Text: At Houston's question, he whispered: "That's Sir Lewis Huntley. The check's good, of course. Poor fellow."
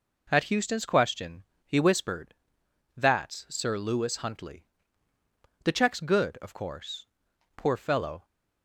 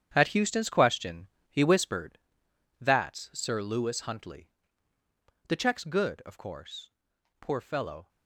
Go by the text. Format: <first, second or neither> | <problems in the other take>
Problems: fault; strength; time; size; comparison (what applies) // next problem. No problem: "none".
first | gets quieter; strong; throughout; 10.5 dB